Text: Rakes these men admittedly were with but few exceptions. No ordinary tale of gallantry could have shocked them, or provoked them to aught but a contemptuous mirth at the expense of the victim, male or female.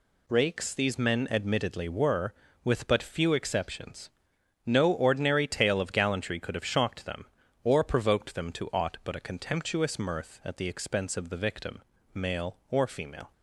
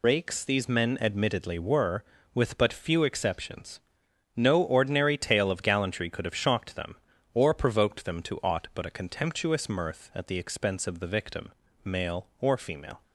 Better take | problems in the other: first | loses the start of "Rakes"; at 0.0 s; 55 ms

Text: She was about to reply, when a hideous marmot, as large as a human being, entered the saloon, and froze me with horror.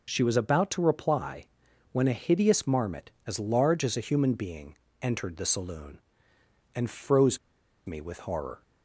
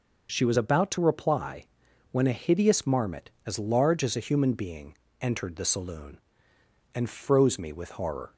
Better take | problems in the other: second | pauses between "froze" and "me"; noticeable; at 7.3 s; 0.48 s long

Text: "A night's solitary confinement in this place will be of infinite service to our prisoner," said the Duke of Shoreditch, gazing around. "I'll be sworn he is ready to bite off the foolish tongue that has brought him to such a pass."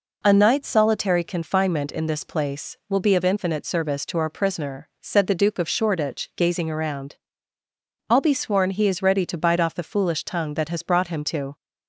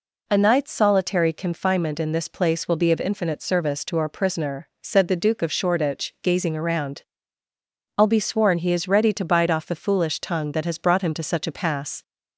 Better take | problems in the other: second | stops before "such a pass"; at 11.5 s

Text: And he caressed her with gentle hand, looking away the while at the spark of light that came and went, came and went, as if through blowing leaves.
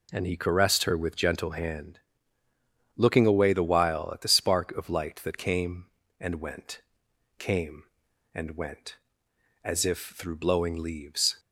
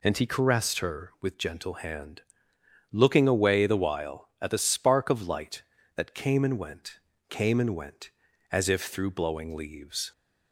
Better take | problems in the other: neither | none

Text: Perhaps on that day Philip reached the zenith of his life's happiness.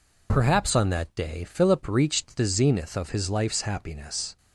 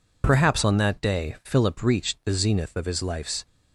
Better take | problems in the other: first | stops before "happiness"; at 3.4 s

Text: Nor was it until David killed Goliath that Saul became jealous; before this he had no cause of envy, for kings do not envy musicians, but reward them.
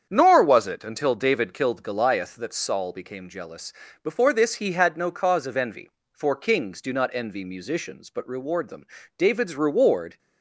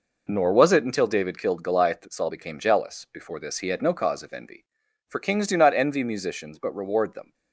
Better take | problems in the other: second | starts louder than the rest; strong; until 1.1 s; 8 dB // goes on to say "David's reward"; noticeable; from 9.1 s on; 1.0 s long

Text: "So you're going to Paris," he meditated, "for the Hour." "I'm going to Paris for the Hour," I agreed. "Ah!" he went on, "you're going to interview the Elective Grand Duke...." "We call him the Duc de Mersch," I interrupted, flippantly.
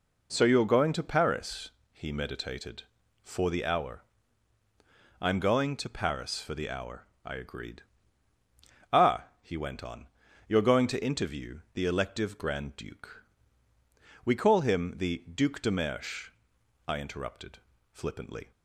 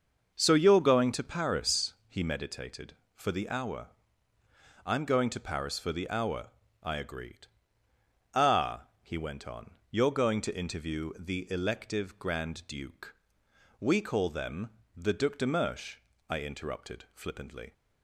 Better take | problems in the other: first | starts louder than the rest; until 1.3 s; 6.5 dB // says "them" for "him"; at 14.3 s

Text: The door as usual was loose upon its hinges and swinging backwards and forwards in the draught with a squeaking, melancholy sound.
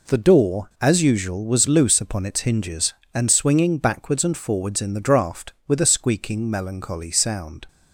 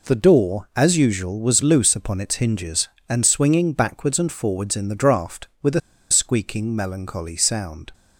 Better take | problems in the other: first | pauses between "a" and "squeaking"; slight; at 5.8 s; 0.30 s long

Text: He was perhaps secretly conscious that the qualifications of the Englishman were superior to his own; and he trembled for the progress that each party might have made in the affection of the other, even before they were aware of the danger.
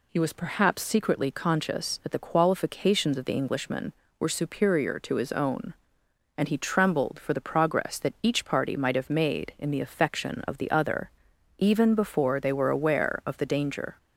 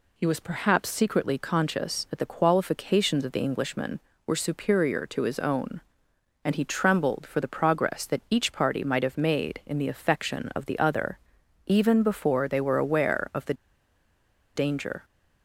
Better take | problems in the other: first | pauses between "the" and "danger"; at 13.5 s; 1.0 s long

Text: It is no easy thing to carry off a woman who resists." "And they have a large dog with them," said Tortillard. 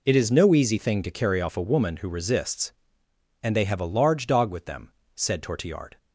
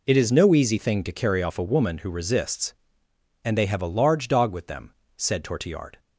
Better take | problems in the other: neither | none

